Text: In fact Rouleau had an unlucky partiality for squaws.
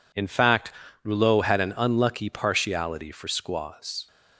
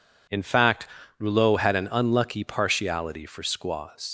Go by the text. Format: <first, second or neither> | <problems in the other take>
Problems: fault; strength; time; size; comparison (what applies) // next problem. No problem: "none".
first | pauses between "fact" and "Rouleau"; slight; at 0.8 s; 0.32 s long; slight in the first // leaves "squaws" unfinished; at 4.0 s; 90 ms